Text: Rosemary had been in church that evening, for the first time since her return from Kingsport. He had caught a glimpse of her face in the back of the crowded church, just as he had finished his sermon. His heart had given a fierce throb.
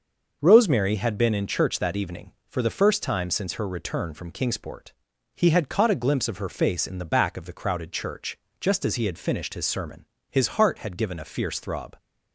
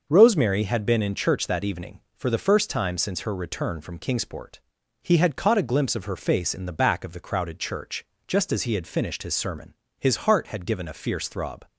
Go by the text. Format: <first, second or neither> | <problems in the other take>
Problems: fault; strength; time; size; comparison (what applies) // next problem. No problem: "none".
neither | starts louder than the rest; the same in both